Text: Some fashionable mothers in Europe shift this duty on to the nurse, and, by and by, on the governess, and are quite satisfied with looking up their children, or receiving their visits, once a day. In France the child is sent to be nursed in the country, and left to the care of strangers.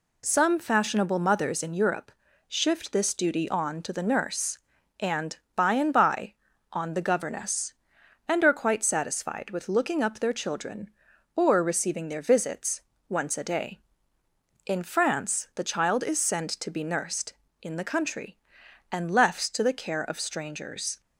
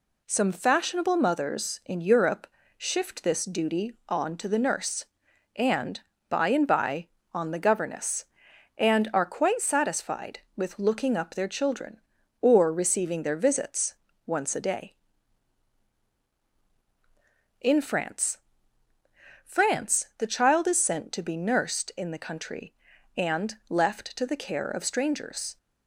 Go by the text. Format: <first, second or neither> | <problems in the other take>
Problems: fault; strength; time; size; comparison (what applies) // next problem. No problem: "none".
first | pauses between "Europe" and "shift"; slight; at 2.4 s; 0.30 s long; also in the first // says "France" twice; at 19.4 s